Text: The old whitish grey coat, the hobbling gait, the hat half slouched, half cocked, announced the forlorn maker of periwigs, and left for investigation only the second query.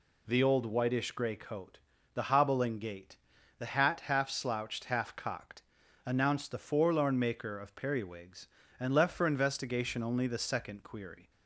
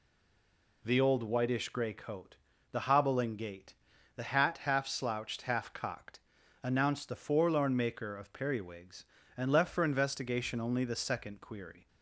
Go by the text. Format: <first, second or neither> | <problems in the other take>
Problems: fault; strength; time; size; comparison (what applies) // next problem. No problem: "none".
first | stays silent before the first word; slight; until 0.8 s; 0.8 s long